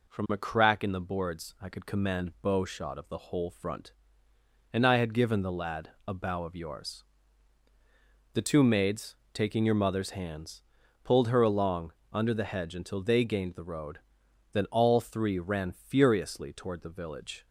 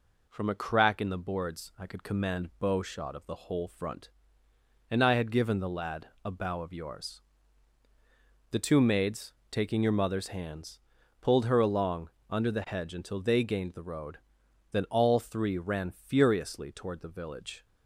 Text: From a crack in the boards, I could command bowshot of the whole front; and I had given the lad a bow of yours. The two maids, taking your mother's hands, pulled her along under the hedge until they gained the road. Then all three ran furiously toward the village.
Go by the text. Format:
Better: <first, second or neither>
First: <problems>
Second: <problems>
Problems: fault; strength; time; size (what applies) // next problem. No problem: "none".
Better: neither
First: pauses between "lad" and "a"; slight; at 5.9 s; 0.16 s long // pauses between "along" and "under"; slight; at 11.9 s; 0.20 s long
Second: pauses between "lad" and "a"; slight; at 6.0 s; 0.16 s long // pauses between "along" and "under"; slight; at 12.0 s; 0.20 s long